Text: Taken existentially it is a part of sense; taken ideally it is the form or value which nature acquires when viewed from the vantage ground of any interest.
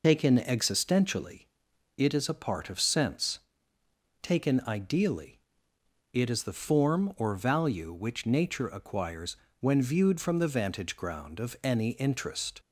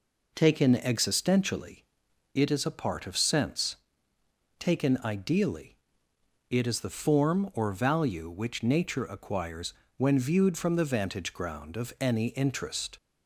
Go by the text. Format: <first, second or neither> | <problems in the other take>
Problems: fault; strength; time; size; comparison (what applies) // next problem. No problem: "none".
second | loses the start of "Taken"; at 0.0 s; 70 ms // pauses between "existentially" and "it"; noticeable; at 1.4 s; 0.52 s long; noticeable in the second // pauses between "ideally" and "it"; noticeable; at 5.3 s; 0.72 s long; noticeable in the second // pauses between "acquires" and "when"; slight; at 9.3 s; 0.24 s long; slight in the second